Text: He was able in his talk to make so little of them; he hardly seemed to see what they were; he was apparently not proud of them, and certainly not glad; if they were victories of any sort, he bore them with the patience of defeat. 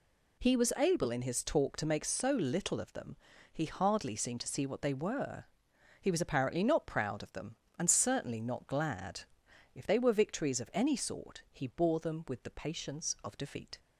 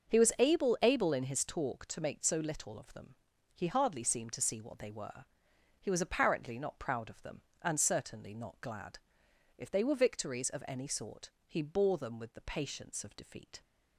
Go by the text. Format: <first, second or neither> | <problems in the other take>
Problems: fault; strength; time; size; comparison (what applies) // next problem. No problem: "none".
first | starts louder than the rest; until 1.1 s; 6.5 dB // says "able" twice; at 0.8 s